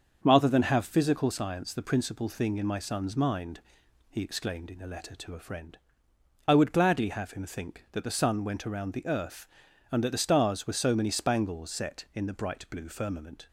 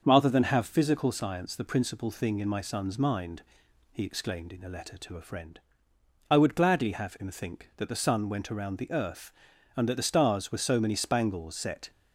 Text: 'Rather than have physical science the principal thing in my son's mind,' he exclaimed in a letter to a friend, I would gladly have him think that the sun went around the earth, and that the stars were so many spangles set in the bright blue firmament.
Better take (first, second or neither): first